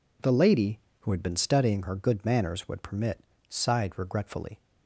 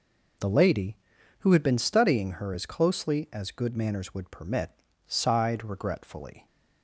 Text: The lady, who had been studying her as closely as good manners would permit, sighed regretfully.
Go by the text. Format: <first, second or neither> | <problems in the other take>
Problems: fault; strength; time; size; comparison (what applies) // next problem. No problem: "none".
second | skips "as closely as"; at 1.9 s